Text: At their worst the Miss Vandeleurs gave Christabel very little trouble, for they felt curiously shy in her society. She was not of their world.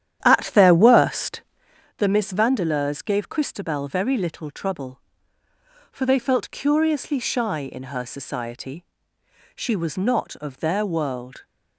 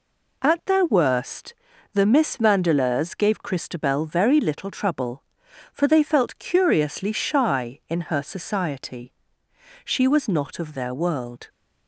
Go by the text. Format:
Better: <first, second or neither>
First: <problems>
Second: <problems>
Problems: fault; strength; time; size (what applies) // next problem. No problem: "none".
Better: second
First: starts louder than the rest; strong; until 1.8 s; 10.5 dB // pauses between "worst" and "the"; noticeable; at 1.4 s; 0.56 s long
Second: pauses between "worst" and "the"; at 1.5 s; 0.38 s long